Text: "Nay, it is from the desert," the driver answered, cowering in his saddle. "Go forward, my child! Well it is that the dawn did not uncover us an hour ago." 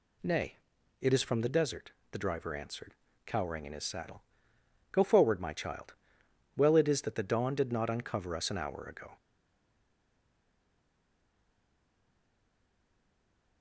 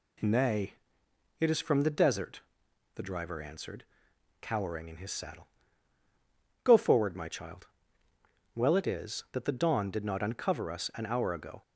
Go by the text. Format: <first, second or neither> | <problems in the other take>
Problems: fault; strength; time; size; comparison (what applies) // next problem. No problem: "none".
second | stays silent after the last word; strong; from 9.1 s on; 4.5 s long